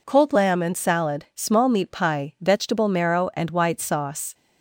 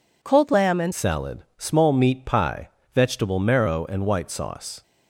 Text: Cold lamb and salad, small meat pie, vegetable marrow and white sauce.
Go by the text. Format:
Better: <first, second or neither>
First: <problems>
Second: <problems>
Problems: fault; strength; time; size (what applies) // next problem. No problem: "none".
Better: first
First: none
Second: changes voice at "salad"; from 0.9 s on; 3.9 s long